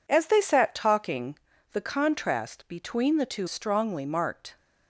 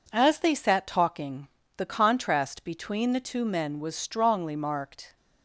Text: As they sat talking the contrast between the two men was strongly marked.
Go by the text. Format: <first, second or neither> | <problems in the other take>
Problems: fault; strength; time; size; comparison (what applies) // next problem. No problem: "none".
second | pauses between "talking" and "the"; at 1.3 s; 0.38 s long; slight in the second // skips "men was"; at 3.4 s